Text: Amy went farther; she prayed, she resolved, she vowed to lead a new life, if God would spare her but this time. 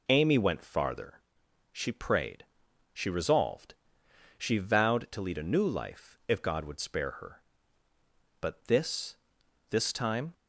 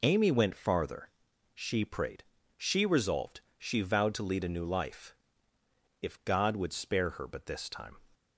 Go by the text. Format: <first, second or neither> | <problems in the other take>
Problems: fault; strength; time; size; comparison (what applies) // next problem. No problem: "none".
second | says "this" twice; at 9.6 s